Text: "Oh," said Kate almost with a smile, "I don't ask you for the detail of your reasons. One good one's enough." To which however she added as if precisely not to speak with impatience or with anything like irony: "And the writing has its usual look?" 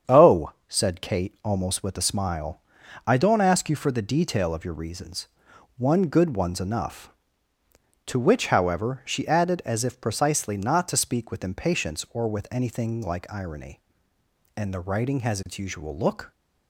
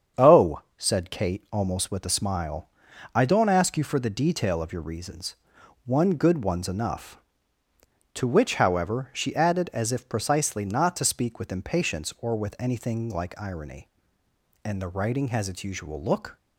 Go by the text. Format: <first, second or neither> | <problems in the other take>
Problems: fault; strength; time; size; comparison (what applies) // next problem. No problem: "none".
neither | starts louder than the rest; strong; the same in both